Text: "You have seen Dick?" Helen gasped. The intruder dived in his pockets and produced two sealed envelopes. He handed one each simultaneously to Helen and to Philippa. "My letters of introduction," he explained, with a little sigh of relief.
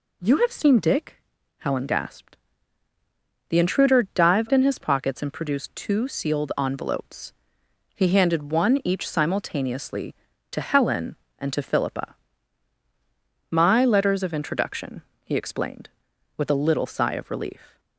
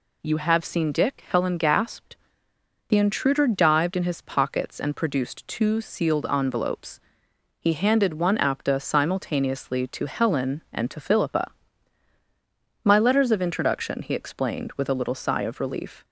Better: first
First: none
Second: says "apta" for "each"; at 8.3 s

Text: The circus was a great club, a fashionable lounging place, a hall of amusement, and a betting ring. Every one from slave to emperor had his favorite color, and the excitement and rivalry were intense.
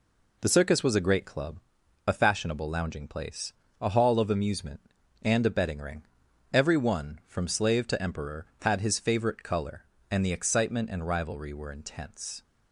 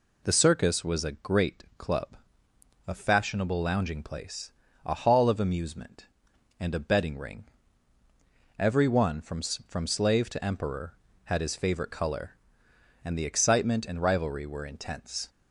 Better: first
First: none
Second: says "from" twice; at 9.4 s

